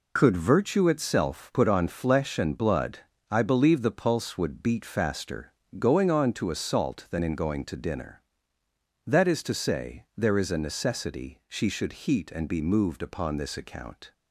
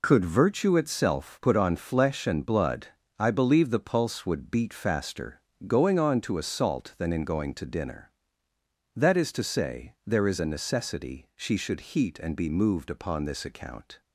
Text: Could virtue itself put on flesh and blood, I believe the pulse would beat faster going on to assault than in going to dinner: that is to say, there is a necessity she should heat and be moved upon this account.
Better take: neither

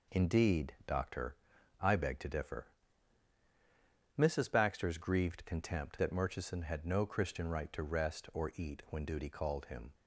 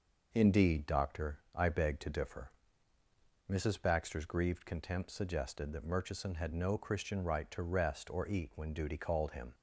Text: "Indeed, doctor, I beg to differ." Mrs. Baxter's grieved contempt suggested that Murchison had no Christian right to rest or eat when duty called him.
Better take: second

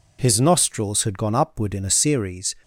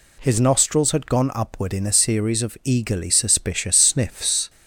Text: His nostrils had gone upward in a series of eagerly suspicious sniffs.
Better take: second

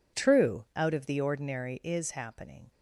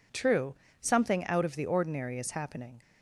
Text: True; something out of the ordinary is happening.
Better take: second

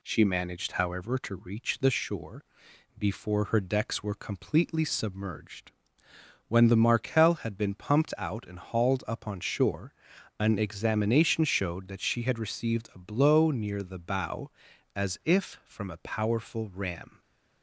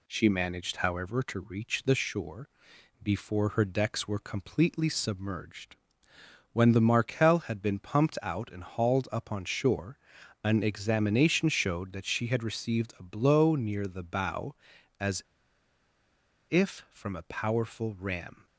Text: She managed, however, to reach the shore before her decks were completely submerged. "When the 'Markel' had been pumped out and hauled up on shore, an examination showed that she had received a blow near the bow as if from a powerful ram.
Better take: first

